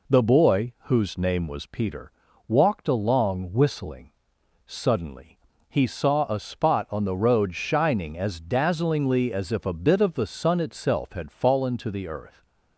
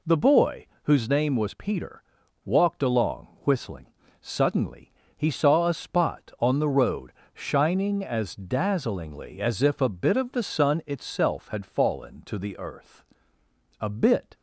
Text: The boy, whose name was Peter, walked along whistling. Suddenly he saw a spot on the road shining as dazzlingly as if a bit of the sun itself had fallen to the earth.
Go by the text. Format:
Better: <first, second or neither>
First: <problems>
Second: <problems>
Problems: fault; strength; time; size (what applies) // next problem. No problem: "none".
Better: first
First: pauses between "Suddenly" and "he"; slight; at 5.3 s; 0.28 s long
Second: pauses between "along" and "whistling"; slight; at 3.2 s; 0.16 s long // pauses between "Suddenly" and "he"; slight; at 4.9 s; 0.24 s long // pauses between "road" and "shining"; slight; at 7.1 s; 0.22 s long // goes on to say "A bit"; from 13.7 s on; 0.54 s long